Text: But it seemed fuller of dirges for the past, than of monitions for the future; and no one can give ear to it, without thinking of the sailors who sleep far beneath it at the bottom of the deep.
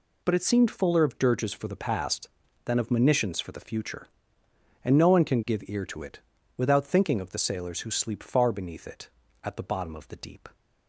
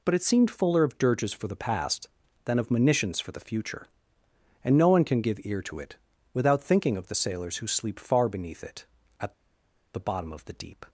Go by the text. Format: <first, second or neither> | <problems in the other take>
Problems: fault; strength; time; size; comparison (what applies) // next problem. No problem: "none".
first | pauses between "at" and "the"; noticeable; at 9.3 s; 0.63 s long